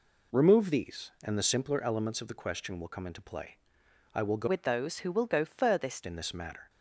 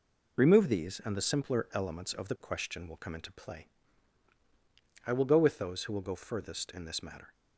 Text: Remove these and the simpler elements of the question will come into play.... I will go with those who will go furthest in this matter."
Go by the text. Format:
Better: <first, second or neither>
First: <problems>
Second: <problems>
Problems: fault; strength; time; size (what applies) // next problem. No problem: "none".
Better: second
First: changes voice from "with" to "furthest"; from 4.4 to 6.0 s; 1.6 s long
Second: none